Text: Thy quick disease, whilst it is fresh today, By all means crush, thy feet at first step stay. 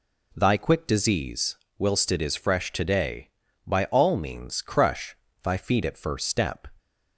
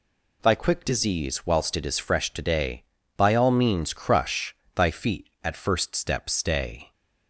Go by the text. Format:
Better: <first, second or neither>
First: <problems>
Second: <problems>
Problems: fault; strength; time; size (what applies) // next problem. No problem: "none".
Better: second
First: stops before "stay"; at 6.7 s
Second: none